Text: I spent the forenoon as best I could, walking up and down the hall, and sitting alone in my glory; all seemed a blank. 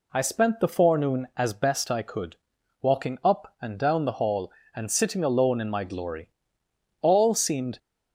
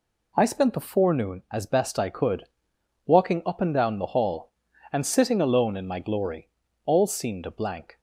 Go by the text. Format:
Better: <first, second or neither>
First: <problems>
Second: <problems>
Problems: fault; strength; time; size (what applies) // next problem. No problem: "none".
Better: second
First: stops before "a blank"; at 7.7 s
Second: none